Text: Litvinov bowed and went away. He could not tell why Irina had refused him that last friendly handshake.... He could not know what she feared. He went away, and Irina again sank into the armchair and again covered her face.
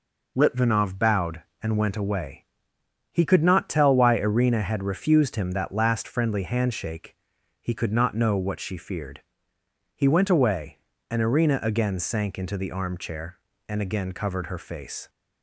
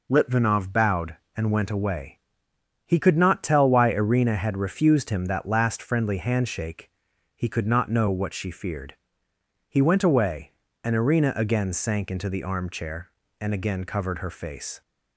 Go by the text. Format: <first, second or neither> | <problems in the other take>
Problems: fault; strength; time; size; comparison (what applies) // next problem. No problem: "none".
neither | none